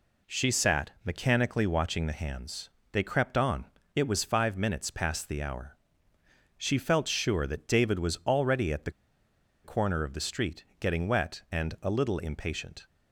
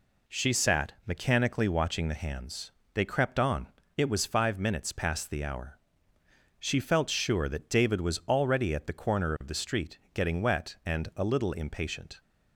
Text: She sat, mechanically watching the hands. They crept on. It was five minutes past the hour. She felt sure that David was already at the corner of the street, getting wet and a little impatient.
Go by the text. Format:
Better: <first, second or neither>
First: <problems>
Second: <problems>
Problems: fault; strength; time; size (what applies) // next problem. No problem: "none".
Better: second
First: pauses between "the" and "corner"; noticeable; at 8.9 s; 0.73 s long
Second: none